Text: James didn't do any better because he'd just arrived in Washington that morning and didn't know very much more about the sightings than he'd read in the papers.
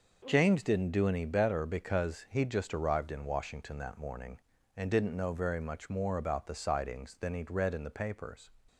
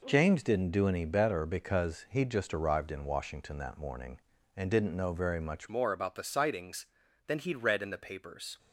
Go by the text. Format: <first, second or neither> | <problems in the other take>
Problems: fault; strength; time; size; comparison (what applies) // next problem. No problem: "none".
first | changes voice at "more"; from 5.6 s on; 2.9 s long